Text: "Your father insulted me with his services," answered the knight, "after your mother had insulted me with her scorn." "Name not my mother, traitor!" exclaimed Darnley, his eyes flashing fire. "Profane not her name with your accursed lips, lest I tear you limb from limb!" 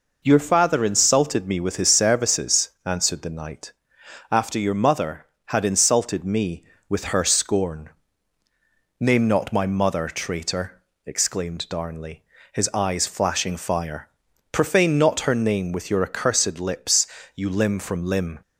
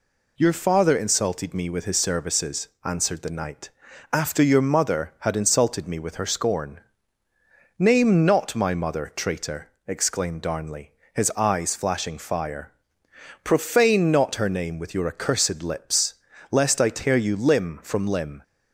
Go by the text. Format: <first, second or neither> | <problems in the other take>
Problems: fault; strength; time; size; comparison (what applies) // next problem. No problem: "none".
second | skips "lest I tear"; at 17.1 s